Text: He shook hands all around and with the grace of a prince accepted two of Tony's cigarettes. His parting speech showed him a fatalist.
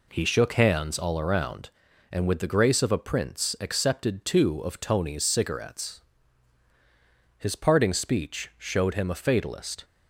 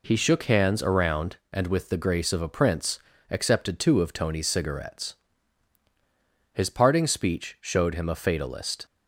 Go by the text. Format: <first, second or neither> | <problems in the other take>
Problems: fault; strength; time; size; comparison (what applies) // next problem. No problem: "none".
first | skips "all"; at 0.8 s // pauses between "prince" and "accepted"; slight; at 2.9 s; 0.32 s long